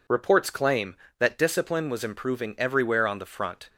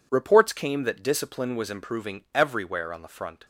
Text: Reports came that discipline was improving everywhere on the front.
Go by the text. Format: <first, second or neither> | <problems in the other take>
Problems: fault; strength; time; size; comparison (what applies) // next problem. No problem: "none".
second | says "claim" for "came"; at 0.4 s